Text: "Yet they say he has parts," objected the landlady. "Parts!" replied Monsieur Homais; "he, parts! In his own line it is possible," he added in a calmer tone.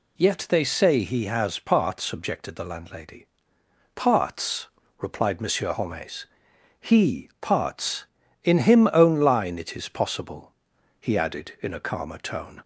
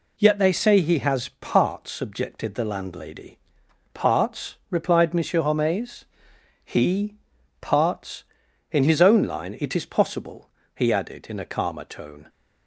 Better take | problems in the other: second | says "him" for "his"; at 8.5 s

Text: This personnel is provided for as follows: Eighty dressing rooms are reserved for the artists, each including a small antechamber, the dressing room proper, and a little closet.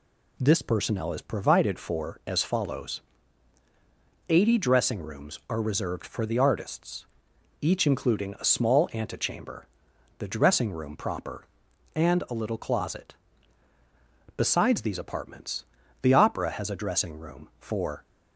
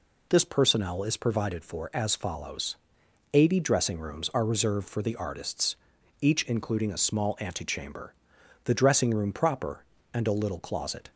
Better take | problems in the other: second | goes on to say "Besides these apartments the Opera has a dressing room for"; strong; from 14.3 s on; 3.6 s long

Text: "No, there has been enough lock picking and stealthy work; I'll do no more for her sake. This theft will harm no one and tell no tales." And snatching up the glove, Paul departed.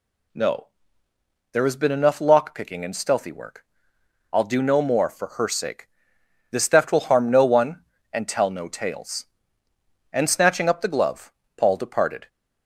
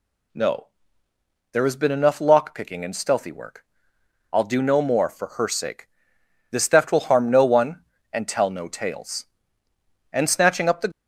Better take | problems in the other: first | stops before "glove Paul departed"; at 10.9 s

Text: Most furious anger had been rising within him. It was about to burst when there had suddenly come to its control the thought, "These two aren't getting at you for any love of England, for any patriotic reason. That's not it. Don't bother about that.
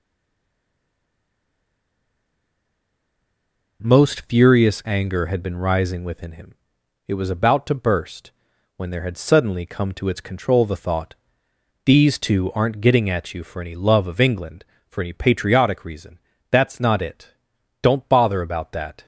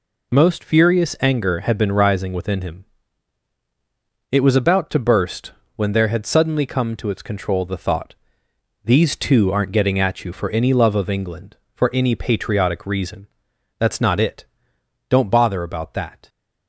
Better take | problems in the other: second | stays silent before the first word; strong; until 3.8 s; 3.8 s long // pauses between "burst" and "when"; noticeable; at 8.2 s; 0.48 s long; slight in the second

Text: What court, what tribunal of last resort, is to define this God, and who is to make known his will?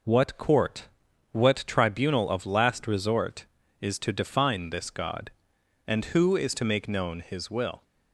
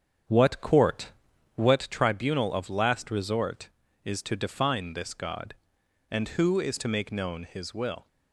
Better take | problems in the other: first | starts louder than the rest; strong; until 1.9 s; 7.5 dB

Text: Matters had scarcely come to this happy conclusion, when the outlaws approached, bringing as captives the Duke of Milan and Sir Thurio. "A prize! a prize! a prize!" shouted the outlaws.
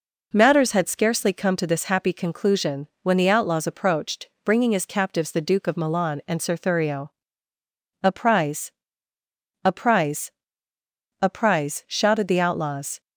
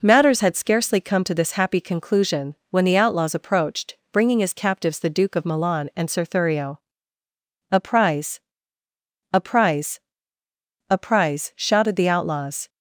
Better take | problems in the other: neither | none

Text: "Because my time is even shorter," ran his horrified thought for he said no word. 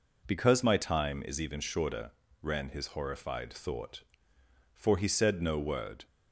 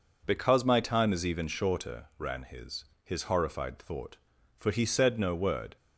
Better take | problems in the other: first | says "his" twice; at 3.0 s

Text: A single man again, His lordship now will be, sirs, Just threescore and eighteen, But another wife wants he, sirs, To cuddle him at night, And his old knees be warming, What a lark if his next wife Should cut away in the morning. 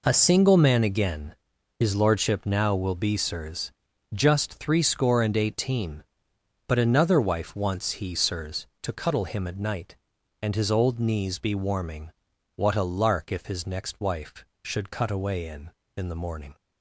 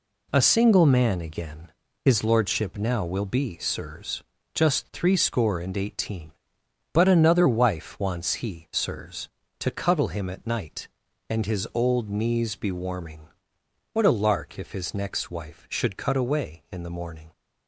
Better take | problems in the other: second | says "in" twice; at 15.9 s

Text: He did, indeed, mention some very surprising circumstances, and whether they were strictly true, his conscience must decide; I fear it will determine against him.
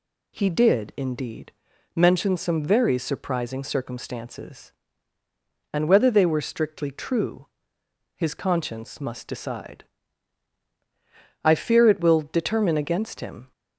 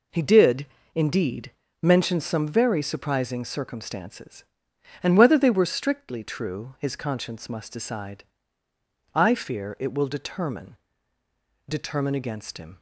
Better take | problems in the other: first | says "determine" twice; at 11.6 s

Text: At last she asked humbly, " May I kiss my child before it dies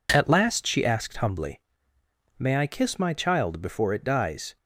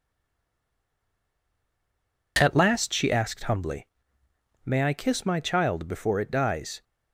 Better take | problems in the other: first | stays silent before the first word; until 2.3 s; 2.3 s long

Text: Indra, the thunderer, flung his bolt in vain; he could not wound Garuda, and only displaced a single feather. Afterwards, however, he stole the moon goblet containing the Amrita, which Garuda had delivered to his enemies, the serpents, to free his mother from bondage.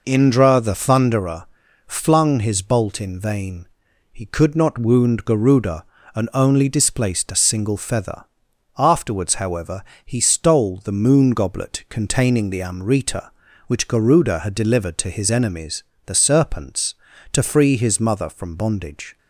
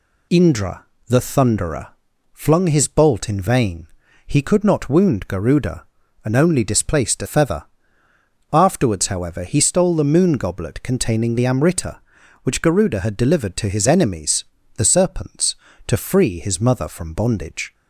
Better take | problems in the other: first | skips "single"; at 7.2 s

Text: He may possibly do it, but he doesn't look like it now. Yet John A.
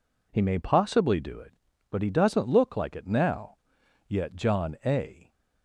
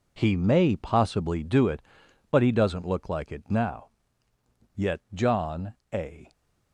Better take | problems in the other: first | gets quieter; strong; throughout; 10.5 dB // pauses between "John" and "A"; slight; at 5.7 s; 0.18 s long

